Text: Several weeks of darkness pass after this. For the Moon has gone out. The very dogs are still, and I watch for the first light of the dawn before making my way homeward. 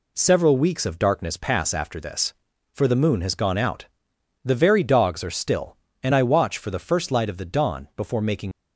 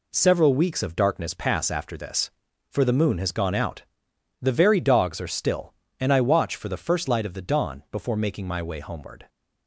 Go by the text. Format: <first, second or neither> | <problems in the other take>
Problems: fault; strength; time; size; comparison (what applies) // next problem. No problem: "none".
second | stops before "my way homeward"; at 8.5 s